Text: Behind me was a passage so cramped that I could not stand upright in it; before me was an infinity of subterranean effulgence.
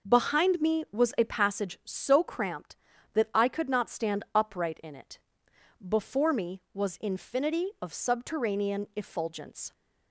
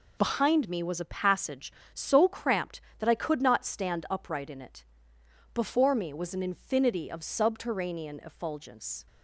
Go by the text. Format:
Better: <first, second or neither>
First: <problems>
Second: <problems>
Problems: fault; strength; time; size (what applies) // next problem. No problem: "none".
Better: second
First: skips "an"; at 6.9 s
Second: none